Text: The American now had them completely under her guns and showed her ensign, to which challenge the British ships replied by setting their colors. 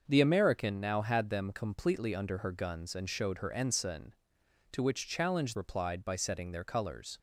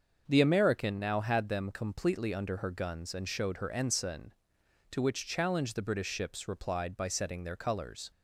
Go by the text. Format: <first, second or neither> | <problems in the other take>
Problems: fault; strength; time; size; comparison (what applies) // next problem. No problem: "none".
second | starts louder than the rest; until 1.0 s; 6 dB; also in the second // skips "the British ships"; at 5.5 s